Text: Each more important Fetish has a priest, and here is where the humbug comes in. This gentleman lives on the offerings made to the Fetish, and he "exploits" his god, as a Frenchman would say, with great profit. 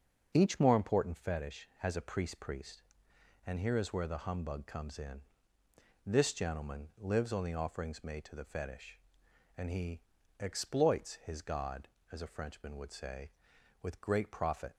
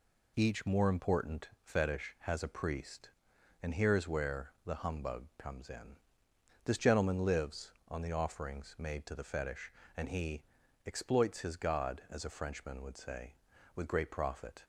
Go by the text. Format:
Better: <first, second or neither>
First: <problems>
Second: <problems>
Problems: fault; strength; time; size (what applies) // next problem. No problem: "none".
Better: second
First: starts louder than the rest; until 1.3 s; 6 dB // says "priest" twice; at 2.4 s // pauses between "he" and "exploits"; at 10.0 s; 0.38 s long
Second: pauses between "he" and "exploits"; at 10.4 s; 0.44 s long